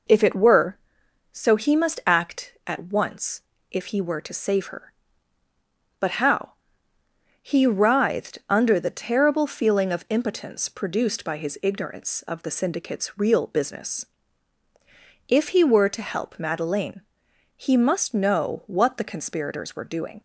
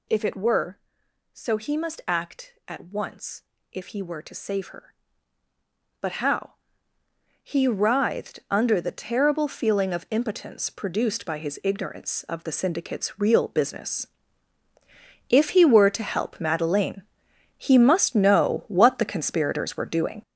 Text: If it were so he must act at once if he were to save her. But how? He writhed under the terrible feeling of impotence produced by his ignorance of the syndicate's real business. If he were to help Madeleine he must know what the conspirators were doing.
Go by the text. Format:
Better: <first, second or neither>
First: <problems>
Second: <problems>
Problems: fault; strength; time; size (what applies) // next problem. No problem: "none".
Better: first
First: pauses between "once" and "if"; slight; at 3.4 s; 0.28 s long // pauses between "Madeleine" and "he"; noticeable; at 17.0 s; 0.54 s long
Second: gets louder; strong; throughout; 8.5 dB // pauses between "once" and "if"; slight; at 3.4 s; 0.28 s long // pauses between "Madeleine" and "he"; noticeable; at 17.0 s; 0.54 s long